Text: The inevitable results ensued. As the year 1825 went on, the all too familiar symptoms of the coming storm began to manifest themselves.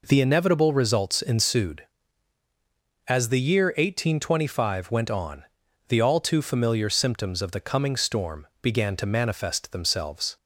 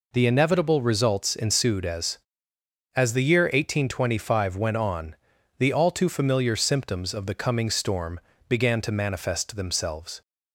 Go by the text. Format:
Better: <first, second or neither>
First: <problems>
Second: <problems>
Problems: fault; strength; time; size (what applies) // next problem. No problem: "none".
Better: first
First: none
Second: says "As" twice; at 2.9 s // pauses between "storm" and "began"; slight; at 8.1 s; 0.28 s long